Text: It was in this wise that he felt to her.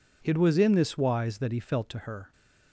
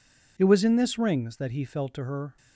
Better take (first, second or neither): first